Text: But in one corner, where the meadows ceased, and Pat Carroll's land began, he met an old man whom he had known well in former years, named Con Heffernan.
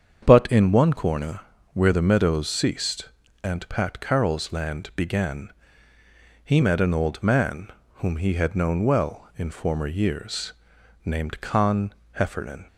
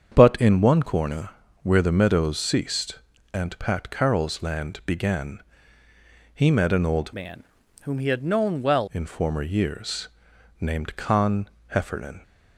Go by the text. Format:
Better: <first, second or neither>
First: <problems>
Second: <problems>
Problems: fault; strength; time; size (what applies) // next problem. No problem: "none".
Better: first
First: starts louder than the rest; strong; until 1.2 s; 7.5 dB // pauses between "man" and "whom"; slight; at 7.6 s; 0.26 s long // pauses between "Con" and "Heffernan"; slight; at 11.9 s; 0.20 s long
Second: starts louder than the rest; strong; until 1.1 s; 7.5 dB // changes voice from "man" to "well"; from 7.1 to 8.8 s; 1.7 s long // pauses between "man" and "whom"; at 7.4 s; 0.38 s long // pauses between "Con" and "Heffernan"; slight; at 11.4 s; 0.20 s long